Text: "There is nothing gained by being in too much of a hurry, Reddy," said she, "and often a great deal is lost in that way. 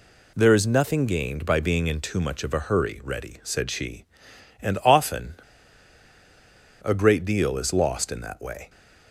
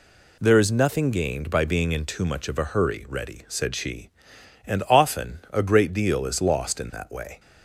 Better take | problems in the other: second | pauses between "often" and "a"; strong; at 5.3 s; 1.4 s long

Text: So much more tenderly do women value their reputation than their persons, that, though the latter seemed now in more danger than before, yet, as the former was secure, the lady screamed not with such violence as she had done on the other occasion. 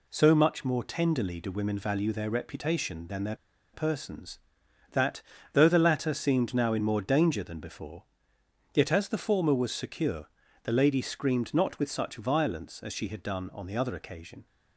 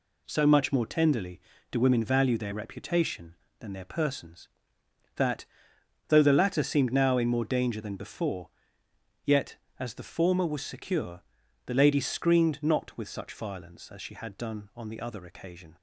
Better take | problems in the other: second | pauses between "their" and "persons"; at 3.3 s; 0.38 s long

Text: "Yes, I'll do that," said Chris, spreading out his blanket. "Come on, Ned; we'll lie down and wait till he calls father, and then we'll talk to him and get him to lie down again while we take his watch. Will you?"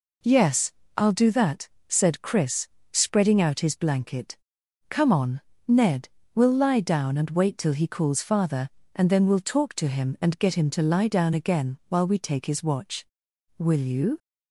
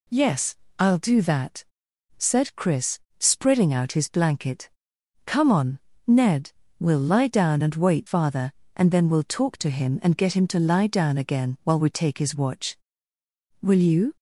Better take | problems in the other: first | skips "till he calls"; at 8.0 s

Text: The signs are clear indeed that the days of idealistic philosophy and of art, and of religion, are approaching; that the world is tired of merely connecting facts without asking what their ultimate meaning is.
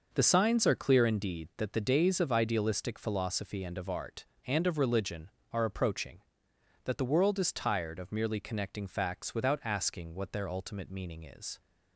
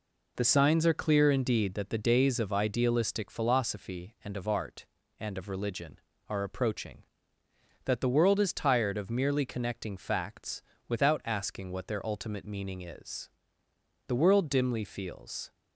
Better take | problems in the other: first | pauses between "facts" and "without"; slight; at 10.6 s; 0.28 s long // goes on to say "The world dimly feels"; from 14.0 s on; 1.4 s long

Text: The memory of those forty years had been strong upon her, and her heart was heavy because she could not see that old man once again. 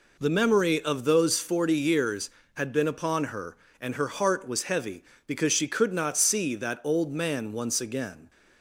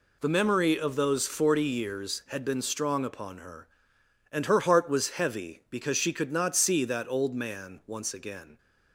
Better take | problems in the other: second | skips "strong"; at 2.8 s

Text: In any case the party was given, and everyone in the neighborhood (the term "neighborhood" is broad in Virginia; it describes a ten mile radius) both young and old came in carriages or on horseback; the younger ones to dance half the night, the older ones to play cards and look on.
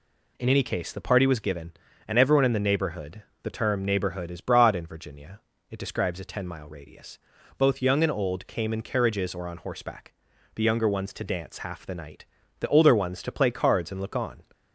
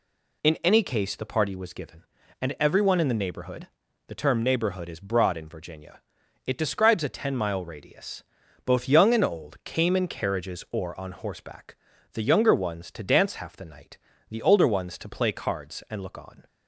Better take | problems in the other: neither | none

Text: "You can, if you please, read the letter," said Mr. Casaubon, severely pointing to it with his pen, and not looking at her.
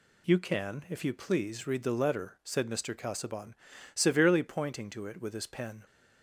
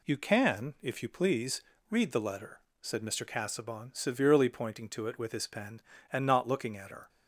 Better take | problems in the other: second | stops before "and not looking at her"; at 5.8 s

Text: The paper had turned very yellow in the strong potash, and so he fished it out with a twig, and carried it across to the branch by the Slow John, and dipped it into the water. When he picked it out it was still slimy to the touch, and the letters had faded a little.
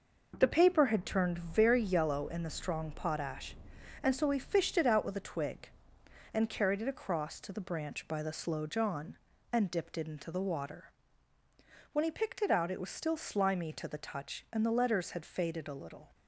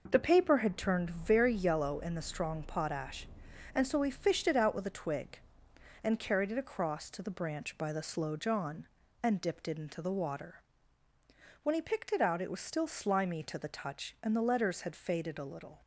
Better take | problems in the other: neither | none

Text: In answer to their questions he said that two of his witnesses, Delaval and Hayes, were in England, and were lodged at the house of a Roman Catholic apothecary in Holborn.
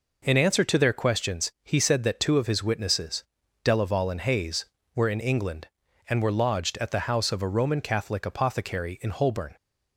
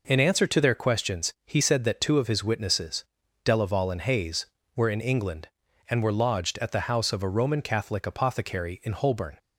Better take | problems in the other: neither | none

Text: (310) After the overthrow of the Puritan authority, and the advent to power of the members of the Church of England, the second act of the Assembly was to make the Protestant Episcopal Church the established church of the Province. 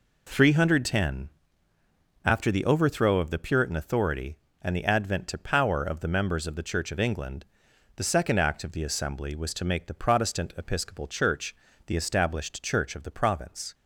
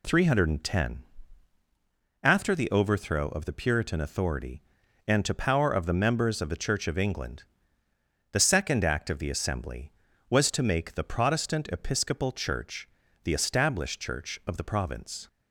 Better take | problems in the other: first | skips "the advent"; at 5.2 s // pauses between "Church" and "the"; slight; at 12.8 s; 0.36 s long; slight in the first

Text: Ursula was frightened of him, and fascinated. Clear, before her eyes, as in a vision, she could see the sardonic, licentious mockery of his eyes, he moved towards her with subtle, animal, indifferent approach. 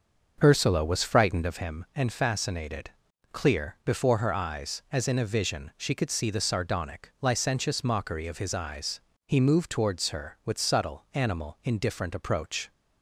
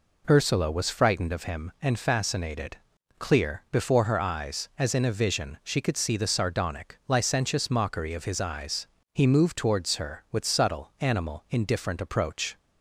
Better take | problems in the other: second | starts louder than the rest; until 1.7 s; 6.5 dB

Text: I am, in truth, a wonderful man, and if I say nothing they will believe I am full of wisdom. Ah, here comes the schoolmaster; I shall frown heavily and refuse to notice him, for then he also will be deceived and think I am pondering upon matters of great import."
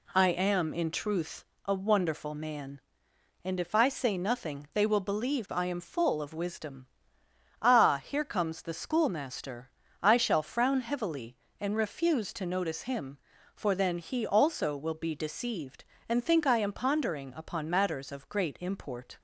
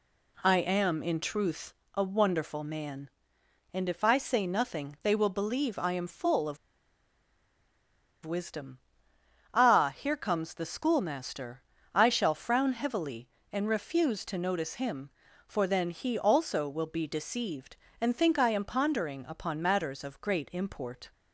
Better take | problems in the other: first | pauses between "of" and "wisdom"; strong; at 6.5 s; 1.6 s long

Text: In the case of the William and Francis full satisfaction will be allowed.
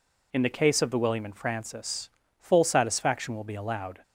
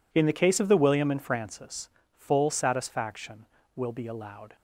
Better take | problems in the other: neither | pauses between "Francis" and "full"; slight; the same in both

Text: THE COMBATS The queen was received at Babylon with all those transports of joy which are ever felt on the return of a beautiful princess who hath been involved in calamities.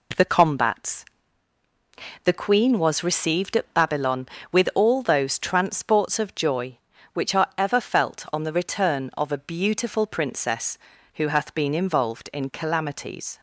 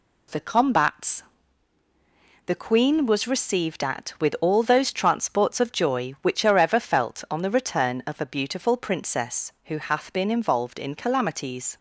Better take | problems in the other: first | pauses between "COMBATS" and "The"; at 1.2 s; 1.2 s long; also in the first // skips "Babylon"; at 4.1 s

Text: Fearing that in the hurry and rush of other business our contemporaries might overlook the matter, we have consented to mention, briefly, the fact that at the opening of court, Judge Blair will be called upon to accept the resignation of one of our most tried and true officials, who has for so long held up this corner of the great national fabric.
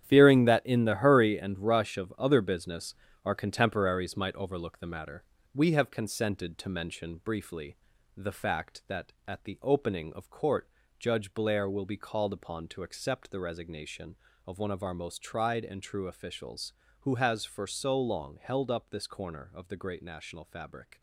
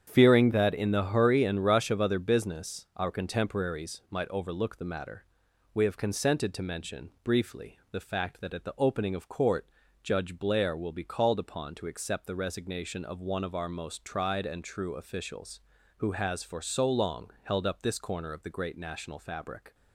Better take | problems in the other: second | gets quieter; strong; throughout; 10.5 dB // starts louder than the rest; strong; until 1.0 s; 10 dB; strong in the second // pauses between "business" and "our"; slight; at 2.9 s; 0.30 s long

